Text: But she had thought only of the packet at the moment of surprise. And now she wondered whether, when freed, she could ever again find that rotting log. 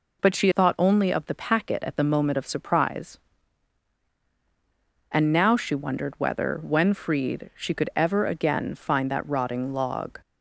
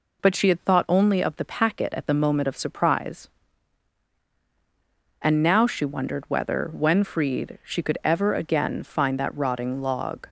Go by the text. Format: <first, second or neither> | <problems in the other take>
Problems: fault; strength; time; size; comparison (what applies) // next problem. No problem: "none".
second | skips "had"; at 0.5 s